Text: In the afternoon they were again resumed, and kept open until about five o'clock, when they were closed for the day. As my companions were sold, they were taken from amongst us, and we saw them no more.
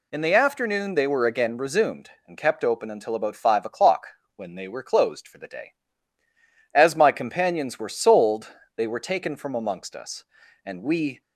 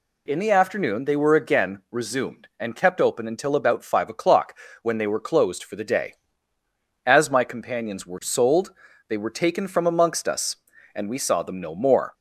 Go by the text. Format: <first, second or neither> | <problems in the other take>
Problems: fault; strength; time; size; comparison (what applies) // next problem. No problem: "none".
second | stops before "saw them no more"; at 11.2 s